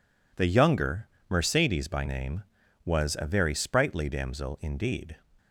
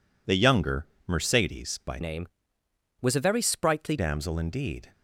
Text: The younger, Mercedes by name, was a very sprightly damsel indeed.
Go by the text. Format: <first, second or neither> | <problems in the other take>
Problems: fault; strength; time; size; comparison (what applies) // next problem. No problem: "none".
first | changes voice from "name" to "sprightly"; from 2.0 to 3.9 s; 1.9 s long